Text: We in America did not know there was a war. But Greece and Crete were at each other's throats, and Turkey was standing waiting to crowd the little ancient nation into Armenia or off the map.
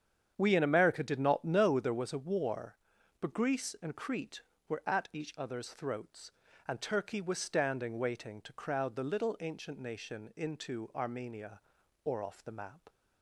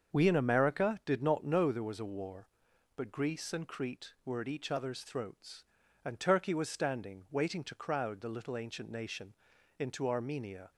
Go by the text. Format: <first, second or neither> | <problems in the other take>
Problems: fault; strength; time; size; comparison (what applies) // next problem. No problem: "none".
first | starts louder than the rest; until 1.2 s; 6.5 dB; strong in the first // pauses between "nation" and "into"; noticeable; at 9.3 s; 0.46 s long // stops before "or off the map"; at 10.7 s